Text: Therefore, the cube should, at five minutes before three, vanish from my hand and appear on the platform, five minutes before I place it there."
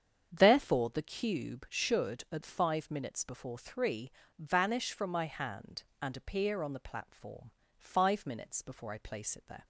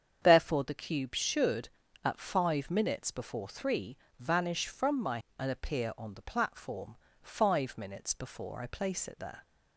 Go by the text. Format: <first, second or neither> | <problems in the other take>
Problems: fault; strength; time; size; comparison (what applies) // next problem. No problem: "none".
first | starts louder than the rest; strong; until 1.2 s; 7.5 dB; strong in the first // skips "hand"; at 5.2 s